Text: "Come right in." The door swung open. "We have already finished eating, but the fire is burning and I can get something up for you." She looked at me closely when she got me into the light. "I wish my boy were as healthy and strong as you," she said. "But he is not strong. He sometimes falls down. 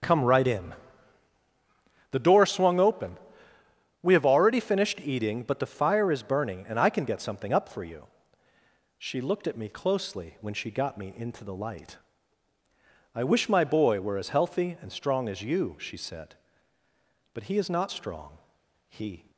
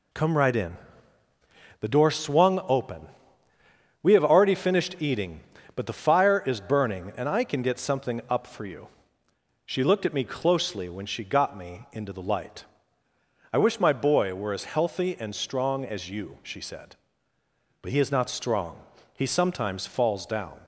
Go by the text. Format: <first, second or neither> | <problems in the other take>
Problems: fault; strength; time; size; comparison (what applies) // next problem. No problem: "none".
second | starts louder than the rest; strong; until 2.4 s; 7.5 dB // stops before "sometimes falls down"; at 19.3 s